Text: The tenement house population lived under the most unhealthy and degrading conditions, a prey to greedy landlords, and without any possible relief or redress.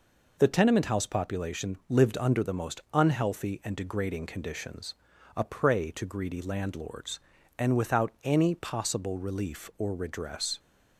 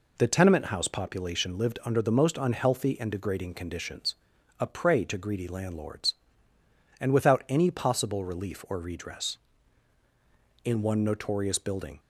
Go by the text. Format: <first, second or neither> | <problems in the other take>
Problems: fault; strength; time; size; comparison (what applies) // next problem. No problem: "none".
first | goes on to say "In one notorious building"; from 10.6 s on; 1.3 s long